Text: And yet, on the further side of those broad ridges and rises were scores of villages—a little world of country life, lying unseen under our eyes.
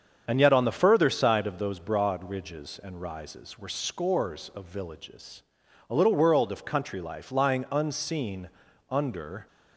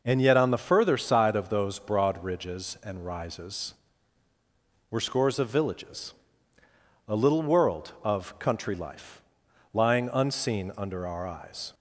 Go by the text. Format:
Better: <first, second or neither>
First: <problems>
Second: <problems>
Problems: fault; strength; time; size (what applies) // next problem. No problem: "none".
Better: second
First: starts louder than the rest; strong; until 1.2 s; 7 dB // pauses between "unseen" and "under"; at 8.4 s; 0.42 s long // stops before "our eyes"; at 9.4 s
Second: none